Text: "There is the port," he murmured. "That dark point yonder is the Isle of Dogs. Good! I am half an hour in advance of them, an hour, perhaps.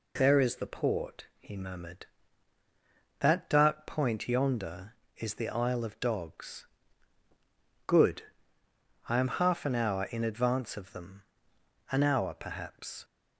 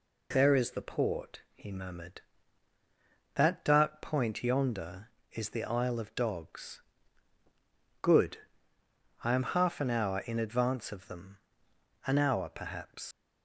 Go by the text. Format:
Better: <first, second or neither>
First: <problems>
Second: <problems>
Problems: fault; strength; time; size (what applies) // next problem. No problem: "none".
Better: first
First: none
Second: leaves "perhaps" unfinished; at 13.1 s; 85 ms